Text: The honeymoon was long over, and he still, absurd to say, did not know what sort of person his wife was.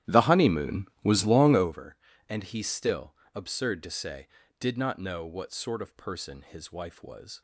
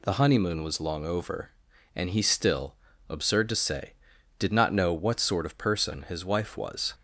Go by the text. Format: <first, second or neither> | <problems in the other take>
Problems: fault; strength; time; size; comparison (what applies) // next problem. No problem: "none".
second | starts louder than the rest; strong; until 1.9 s; 12.5 dB